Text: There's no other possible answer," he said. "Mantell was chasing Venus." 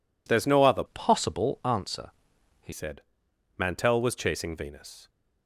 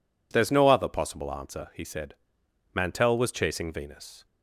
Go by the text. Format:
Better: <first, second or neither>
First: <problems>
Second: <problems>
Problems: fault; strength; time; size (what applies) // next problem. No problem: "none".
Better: second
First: changes voice from "possible" to "he"; from 0.8 to 2.7 s; 1.9 s long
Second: none